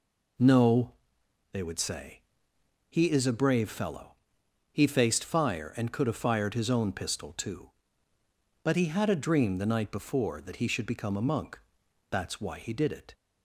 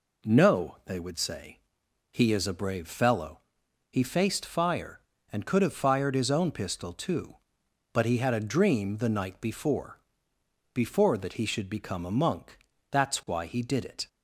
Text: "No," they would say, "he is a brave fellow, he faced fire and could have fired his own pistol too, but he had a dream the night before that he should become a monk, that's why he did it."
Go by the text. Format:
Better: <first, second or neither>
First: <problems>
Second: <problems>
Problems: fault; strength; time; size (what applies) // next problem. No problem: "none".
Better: first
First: none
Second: says "before" twice; at 10.7 s